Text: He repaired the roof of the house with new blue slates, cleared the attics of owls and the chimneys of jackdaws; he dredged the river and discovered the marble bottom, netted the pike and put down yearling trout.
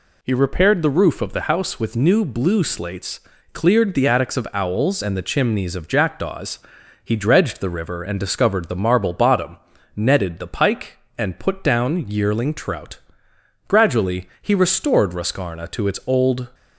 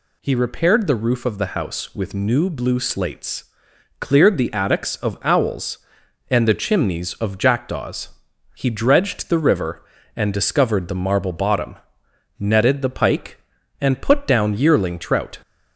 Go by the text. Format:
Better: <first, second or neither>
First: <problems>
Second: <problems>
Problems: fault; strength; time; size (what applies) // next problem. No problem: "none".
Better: second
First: goes on to say "Gradually he restored Roscarna to its old"; strong; from 13.6 s on; 2.8 s long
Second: none